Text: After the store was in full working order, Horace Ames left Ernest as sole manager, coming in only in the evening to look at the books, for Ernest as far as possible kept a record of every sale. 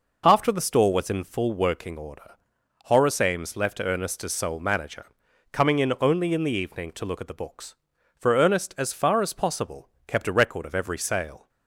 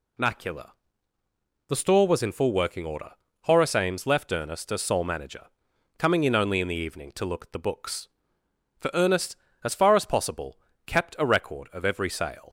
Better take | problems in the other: first | says "Macula" for "After"; at 0.1 s // pauses between "possible" and "kept"; slight; at 10.5 s; 0.28 s long; slight in the first

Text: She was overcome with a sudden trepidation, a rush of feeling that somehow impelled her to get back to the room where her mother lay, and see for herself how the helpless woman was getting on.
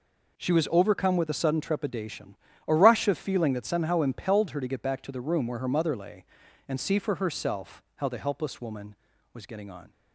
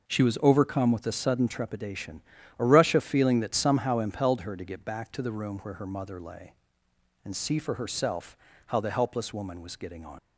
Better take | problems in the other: first | pauses between "herself" and "how"; slight; at 8.3 s; 0.32 s long // leaves "on" unfinished; at 10.1 s; 90 ms

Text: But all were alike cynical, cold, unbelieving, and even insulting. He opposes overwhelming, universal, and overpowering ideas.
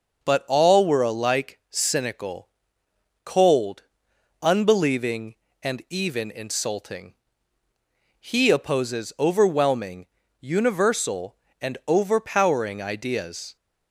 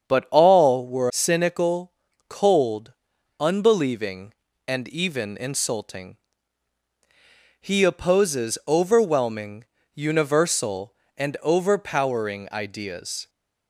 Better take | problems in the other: first | starts louder than the rest; strong; until 1.1 s; 7.5 dB // skips "alike"; at 1.0 s

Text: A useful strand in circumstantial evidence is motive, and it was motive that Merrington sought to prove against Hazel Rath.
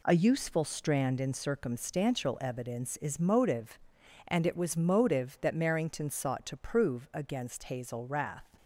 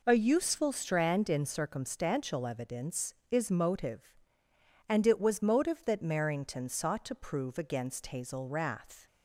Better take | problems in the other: neither | none

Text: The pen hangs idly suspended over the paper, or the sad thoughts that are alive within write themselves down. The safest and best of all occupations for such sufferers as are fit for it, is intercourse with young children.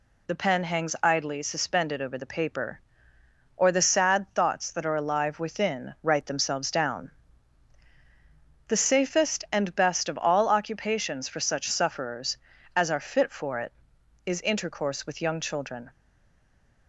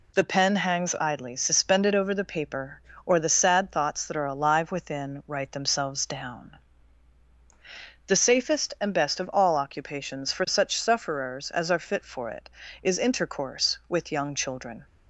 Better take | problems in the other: second | stays silent after the last word; from 15.8 s on; 1.0 s long

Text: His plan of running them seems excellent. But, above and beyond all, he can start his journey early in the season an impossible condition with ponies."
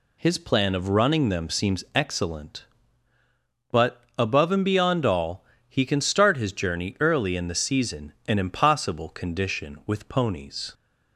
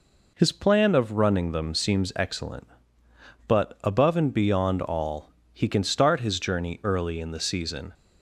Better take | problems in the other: first | stops before "an impossible condition with ponies"; at 7.9 s

